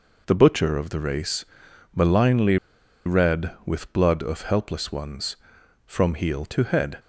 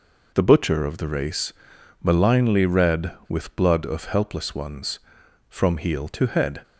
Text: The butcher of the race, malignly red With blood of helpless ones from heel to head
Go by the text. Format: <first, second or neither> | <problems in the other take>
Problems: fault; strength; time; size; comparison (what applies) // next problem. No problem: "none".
second | pauses between "malignly" and "red"; noticeable; at 2.5 s; 0.49 s long